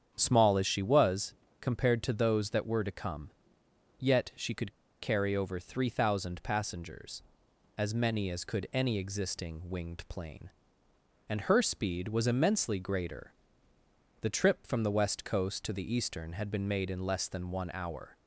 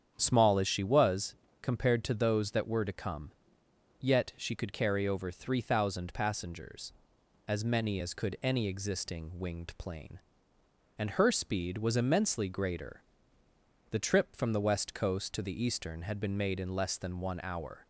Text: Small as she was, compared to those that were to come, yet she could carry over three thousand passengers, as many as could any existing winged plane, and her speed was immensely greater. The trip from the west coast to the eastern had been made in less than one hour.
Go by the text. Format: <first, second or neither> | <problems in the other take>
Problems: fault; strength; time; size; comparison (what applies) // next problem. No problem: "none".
second | starts louder than the rest; strong; until 1.1 s; 8 dB; strong in the second // pauses between "could" and "carry"; slight; at 4.7 s; 0.30 s long